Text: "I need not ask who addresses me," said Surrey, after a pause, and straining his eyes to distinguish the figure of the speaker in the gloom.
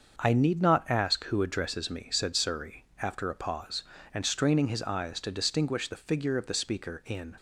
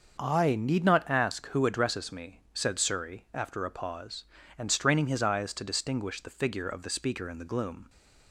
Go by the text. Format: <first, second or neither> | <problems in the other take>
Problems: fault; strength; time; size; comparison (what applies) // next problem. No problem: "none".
second | starts louder than the rest; until 1.1 s; 6.5 dB; noticeable in the second // stops before "the gloom"; at 7.3 s